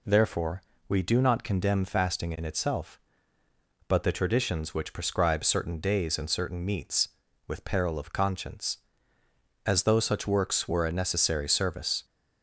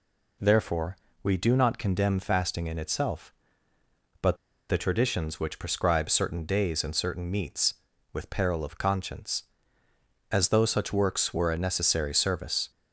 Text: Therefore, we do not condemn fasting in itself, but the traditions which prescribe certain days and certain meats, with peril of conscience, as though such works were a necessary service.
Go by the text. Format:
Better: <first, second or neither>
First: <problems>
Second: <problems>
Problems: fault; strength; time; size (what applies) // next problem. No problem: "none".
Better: first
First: none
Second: pauses between "but" and "the"; slight; at 4.3 s; 0.33 s long